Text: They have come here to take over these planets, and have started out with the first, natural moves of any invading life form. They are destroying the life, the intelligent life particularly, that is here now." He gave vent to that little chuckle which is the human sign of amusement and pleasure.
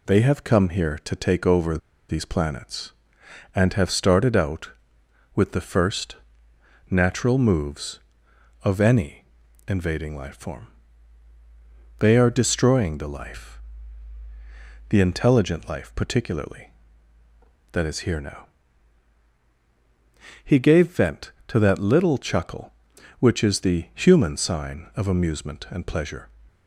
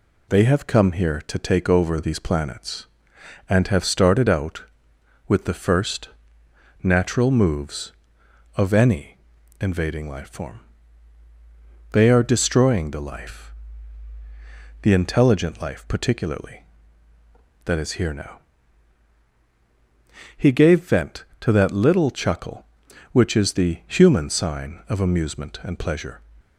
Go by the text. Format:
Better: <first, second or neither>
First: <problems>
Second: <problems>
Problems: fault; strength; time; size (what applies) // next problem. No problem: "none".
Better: second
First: pauses between "over" and "these"; slight; at 1.7 s; 0.31 s long // pauses between "any" and "invading"; at 9.2 s; 0.42 s long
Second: pauses between "any" and "invading"; at 9.1 s; 0.42 s long